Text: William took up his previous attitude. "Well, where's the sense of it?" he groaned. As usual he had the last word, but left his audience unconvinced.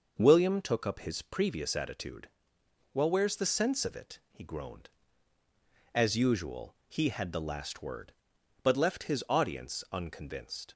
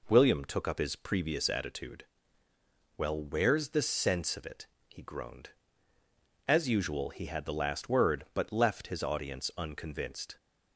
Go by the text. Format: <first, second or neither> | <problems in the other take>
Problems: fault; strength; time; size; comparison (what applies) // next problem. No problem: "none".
neither | none